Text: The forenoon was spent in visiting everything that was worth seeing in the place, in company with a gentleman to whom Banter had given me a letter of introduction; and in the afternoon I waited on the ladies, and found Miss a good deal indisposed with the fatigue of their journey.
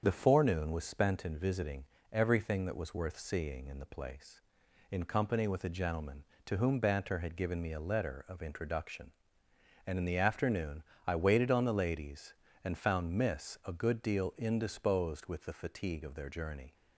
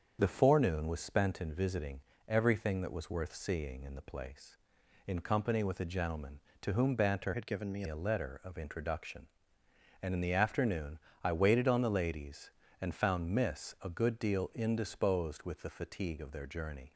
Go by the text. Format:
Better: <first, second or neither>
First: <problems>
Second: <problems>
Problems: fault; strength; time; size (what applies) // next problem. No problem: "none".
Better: first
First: starts louder than the rest; strong; until 1.0 s; 7.5 dB // pauses between "visiting" and "everything"; slight; at 1.8 s; 0.26 s long // pauses between "afternoon" and "I"; slight; at 10.8 s; 0.24 s long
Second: starts louder than the rest; strong; until 1.2 s; 7.5 dB // pauses between "visiting" and "everything"; slight; at 2.0 s; 0.26 s long // changes voice from "had" to "me"; from 7.3 to 7.8 s; 0.5 s long // pauses between "afternoon" and "I"; slight; at 10.9 s; 0.26 s long